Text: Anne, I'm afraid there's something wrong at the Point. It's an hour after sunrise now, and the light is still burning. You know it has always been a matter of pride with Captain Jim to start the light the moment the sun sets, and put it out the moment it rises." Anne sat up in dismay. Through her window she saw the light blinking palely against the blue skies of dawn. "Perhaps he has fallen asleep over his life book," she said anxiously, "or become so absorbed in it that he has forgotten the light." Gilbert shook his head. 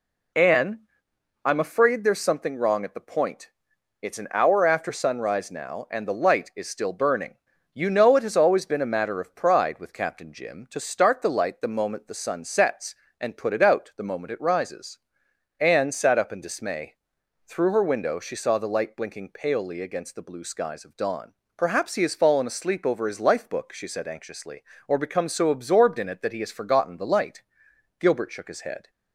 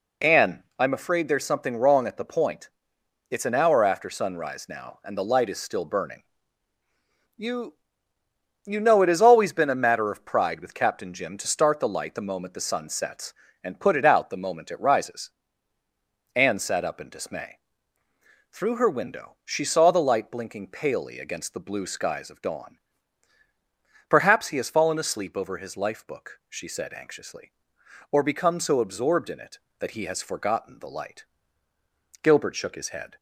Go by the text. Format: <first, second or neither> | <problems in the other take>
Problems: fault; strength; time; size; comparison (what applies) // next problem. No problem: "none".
first | says "You" twice; at 8.6 s